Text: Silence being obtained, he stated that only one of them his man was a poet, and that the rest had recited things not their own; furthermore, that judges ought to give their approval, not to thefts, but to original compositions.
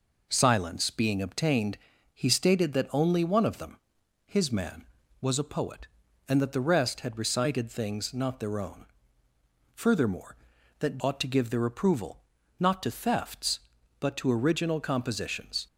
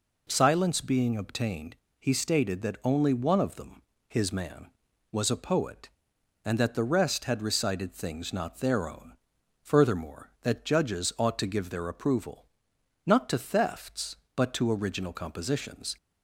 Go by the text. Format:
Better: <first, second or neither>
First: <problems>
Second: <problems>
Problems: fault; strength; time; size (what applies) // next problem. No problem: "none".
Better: second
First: pauses between "them" and "his"; noticeable; at 3.7 s; 0.50 s long // skips "judges"; at 10.9 s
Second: pauses between "them" and "his"; slight; at 3.8 s; 0.26 s long